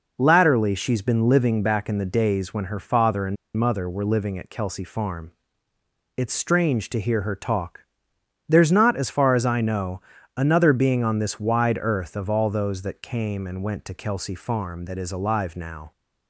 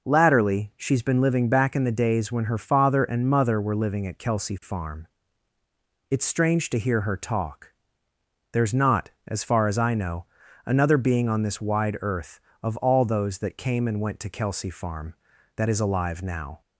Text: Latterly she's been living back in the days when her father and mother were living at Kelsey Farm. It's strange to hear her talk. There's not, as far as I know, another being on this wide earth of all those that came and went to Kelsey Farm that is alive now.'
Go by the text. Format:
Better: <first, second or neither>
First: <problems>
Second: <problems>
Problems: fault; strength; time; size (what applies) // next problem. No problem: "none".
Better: second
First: pauses between "and" and "mother"; slight; at 3.3 s; 0.21 s long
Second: none